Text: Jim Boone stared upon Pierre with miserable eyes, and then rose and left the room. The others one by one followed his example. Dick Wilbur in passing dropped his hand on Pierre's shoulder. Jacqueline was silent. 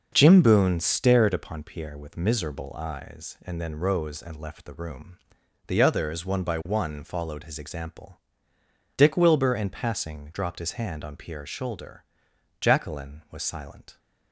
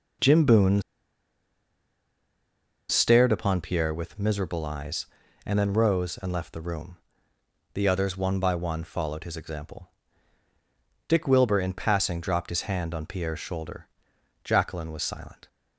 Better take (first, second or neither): first